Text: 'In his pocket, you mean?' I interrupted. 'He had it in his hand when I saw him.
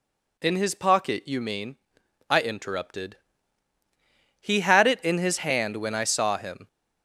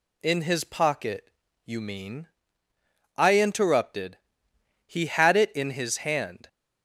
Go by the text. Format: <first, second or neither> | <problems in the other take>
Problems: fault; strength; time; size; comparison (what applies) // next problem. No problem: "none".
first | stops before "when I saw him"; at 6.4 s